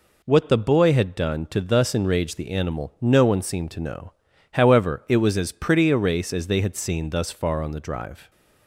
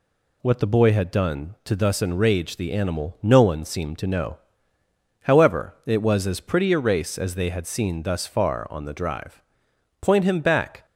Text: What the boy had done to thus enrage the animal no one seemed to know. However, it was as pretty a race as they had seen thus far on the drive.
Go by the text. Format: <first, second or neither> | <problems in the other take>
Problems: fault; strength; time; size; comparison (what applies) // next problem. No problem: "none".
first | goes on to say "Point him back"; noticeable; from 10.0 s on; 0.84 s long